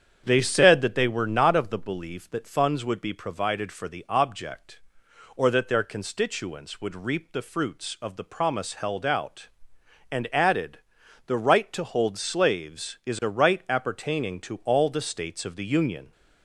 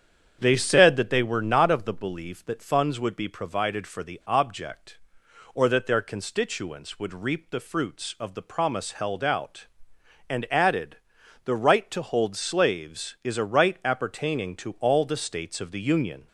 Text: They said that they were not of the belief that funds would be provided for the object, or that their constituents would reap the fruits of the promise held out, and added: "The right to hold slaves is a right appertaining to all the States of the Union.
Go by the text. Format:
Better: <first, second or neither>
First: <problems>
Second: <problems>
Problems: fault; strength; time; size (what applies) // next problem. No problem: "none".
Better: neither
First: starts louder than the rest; strong; until 1.2 s; 8 dB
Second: starts louder than the rest; strong; until 1.4 s; 8 dB